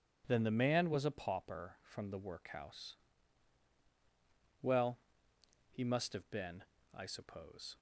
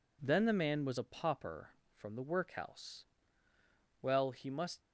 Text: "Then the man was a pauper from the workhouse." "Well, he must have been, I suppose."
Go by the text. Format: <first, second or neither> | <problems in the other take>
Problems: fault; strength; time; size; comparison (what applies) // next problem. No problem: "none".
first | stops before "have been I suppose"; at 4.8 s